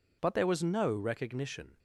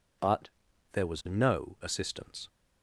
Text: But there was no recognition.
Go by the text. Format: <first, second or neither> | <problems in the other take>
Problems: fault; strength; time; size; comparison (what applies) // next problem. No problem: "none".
first | pauses between "But" and "there"; at 0.4 s; 0.44 s long // says "assistance" for "recognition"; at 1.8 s